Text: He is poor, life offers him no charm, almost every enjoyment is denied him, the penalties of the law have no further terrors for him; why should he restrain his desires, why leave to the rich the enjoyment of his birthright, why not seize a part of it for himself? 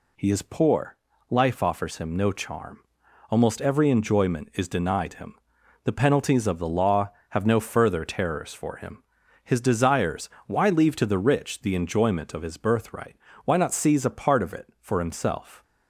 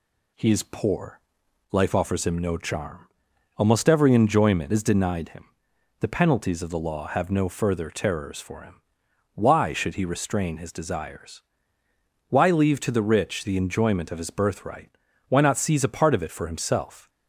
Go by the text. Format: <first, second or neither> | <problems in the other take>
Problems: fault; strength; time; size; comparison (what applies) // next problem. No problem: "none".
second | skips "why should he restrain"; at 9.2 s